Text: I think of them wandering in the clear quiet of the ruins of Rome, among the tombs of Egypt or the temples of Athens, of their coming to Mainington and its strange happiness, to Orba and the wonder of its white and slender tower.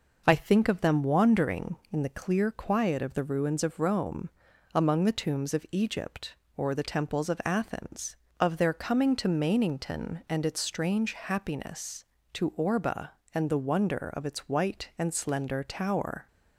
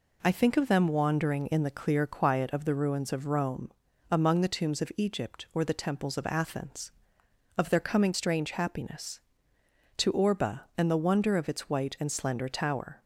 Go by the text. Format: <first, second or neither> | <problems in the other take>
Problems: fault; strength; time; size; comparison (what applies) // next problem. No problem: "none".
first | skips "to Mainington and its"; at 8.1 s